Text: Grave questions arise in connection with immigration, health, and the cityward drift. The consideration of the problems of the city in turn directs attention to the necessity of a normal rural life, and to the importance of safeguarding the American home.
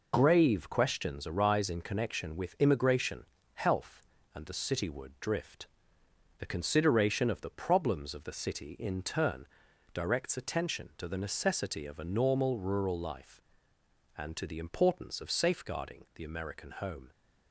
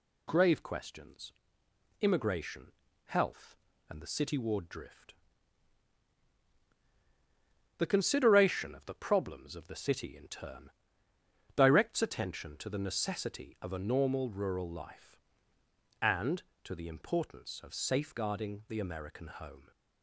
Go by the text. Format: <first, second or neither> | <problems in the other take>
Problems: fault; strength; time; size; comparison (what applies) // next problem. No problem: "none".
first | skips "arise in connection with"; at 1.6 s // pauses between "turn" and "directs"; noticeable; at 10.6 s; 0.86 s long; noticeable in the first